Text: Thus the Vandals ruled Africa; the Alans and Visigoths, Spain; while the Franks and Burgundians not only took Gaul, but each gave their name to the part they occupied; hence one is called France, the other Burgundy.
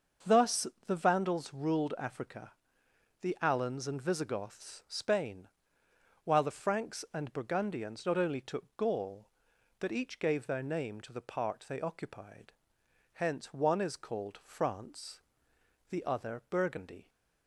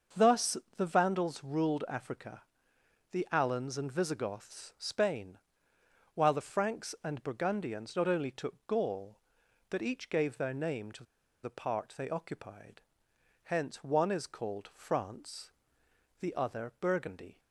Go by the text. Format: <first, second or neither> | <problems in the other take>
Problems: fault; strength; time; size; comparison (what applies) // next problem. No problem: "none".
first | starts louder than the rest; until 1.3 s; 6.5 dB; also in the first // pauses between "Thus" and "the"; slight; at 0.5 s; 0.18 s long; slight in the first // pauses between "to" and "the"; at 11.0 s; 0.39 s long